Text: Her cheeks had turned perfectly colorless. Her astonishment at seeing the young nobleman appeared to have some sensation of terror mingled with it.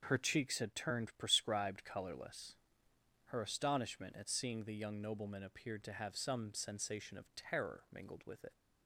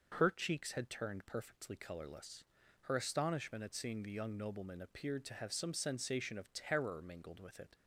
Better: second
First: starts louder than the rest; until 1.0 s; 6.5 dB // says "prescribed" for "perfectly"; at 1.1 s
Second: none

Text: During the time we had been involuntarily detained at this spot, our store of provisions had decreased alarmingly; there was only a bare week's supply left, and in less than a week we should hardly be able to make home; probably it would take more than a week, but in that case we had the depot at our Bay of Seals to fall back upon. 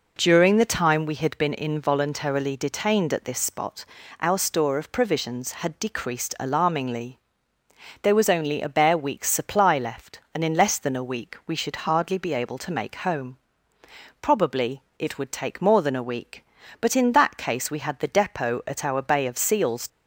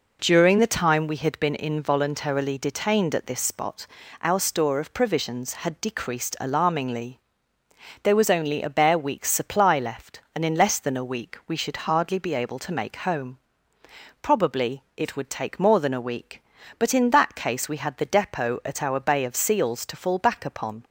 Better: second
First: pauses between "probably" and "it"; slight; at 14.8 s; 0.16 s long // stops before "to fall back upon"; at 19.8 s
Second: none

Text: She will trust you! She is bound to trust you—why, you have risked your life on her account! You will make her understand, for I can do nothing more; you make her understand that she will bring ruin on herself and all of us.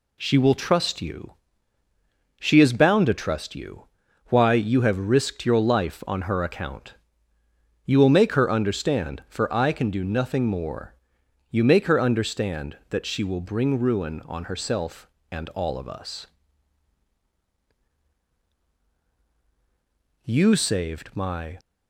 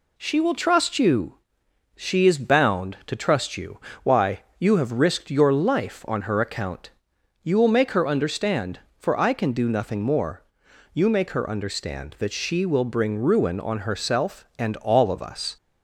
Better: second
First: goes on to say "You saved my"; from 20.2 s on; 1.3 s long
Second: none

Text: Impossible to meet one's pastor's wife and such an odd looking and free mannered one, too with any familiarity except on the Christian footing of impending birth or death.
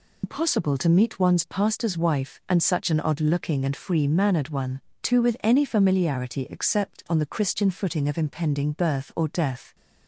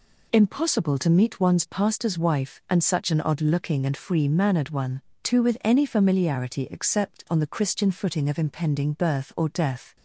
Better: second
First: loses the start of "Impossible"; at 0.2 s; 125 ms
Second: none

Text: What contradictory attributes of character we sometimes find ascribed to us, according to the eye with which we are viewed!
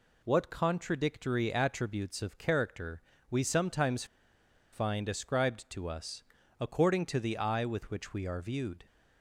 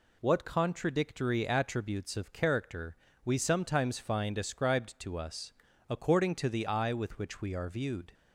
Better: second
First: pauses between "character" and "we"; slight; at 3.0 s; 0.30 s long // pauses between "sometimes" and "find"; noticeable; at 4.0 s; 0.68 s long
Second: pauses between "character" and "we"; slight; at 2.9 s; 0.30 s long

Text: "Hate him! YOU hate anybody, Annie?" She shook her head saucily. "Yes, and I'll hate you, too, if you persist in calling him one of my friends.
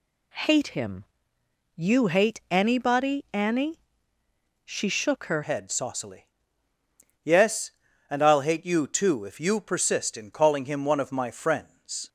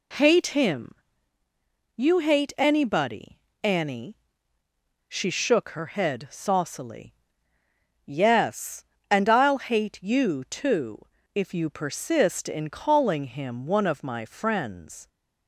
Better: second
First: changes voice at "head"; from 5.4 s on; 6.6 s long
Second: none

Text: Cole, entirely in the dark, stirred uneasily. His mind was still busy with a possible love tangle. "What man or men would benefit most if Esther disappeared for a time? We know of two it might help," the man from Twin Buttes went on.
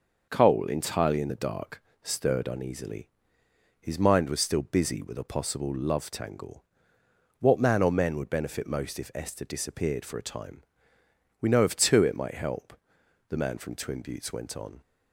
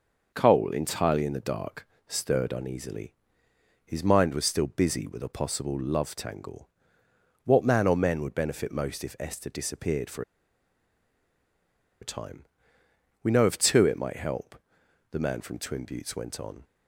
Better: first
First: none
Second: pauses between "for" and "a"; strong; at 10.2 s; 1.7 s long

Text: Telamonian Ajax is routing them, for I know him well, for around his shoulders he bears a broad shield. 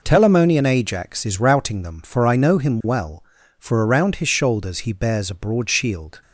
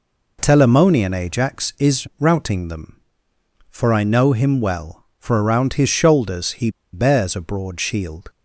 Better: first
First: none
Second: pauses between "he" and "bears"; slight; at 6.6 s; 0.23 s long

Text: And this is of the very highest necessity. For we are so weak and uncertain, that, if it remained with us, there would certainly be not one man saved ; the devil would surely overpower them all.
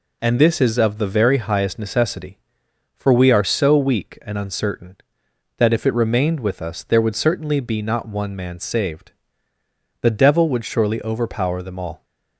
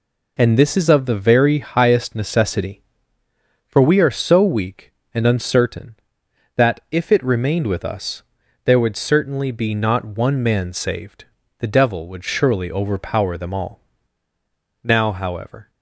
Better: first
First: none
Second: goes on to say "Now however"; noticeable; from 14.8 s on; 0.86 s long

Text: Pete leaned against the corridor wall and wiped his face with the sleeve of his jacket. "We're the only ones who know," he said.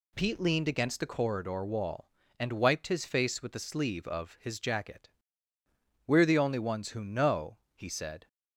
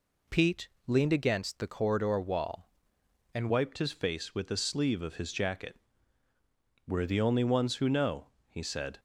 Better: first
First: none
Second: pauses between "Pete" and "leaned"; slight; at 0.6 s; 0.20 s long // changes voice at "wiped"; from 3.4 s on; 5.5 s long

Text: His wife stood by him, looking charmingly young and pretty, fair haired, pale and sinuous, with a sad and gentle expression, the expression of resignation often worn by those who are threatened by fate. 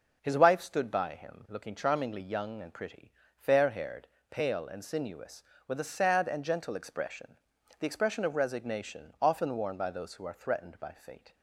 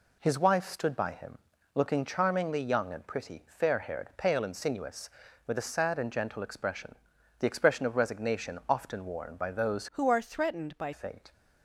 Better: first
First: none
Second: changes voice from "who" to "by"; from 9.9 to 10.9 s; 1.0 s long

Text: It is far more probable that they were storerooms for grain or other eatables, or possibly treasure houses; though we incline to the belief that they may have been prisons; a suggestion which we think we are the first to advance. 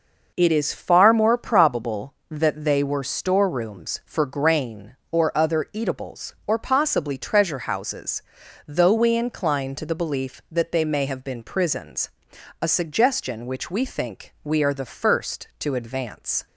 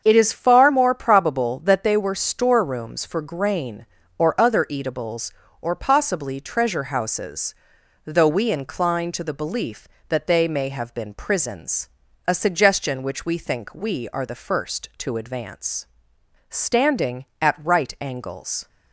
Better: first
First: none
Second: starts louder than the rest; until 1.0 s; 7 dB // goes on to say "Standing at right angles"; strong; from 16.4 s on; 2.2 s long

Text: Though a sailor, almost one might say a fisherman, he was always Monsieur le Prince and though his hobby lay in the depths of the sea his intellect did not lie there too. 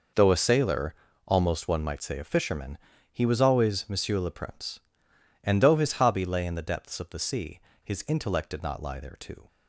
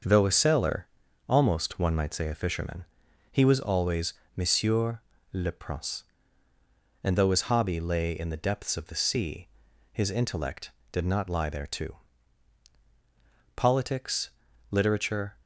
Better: first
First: pauses between "sea" and "his"; slight; at 7.5 s; 0.25 s long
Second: starts louder than the rest; until 1.4 s; 6.5 dB // pauses between "always" and "Monsieur"; slight; at 4.1 s; 0.22 s long // pauses between "Monsieur" and "le"; slight; at 4.9 s; 0.32 s long // pauses between "sea" and "his"; at 9.4 s; 0.44 s long // goes on to say "Politics Literature"; strong; from 13.5 s on; 1.8 s long

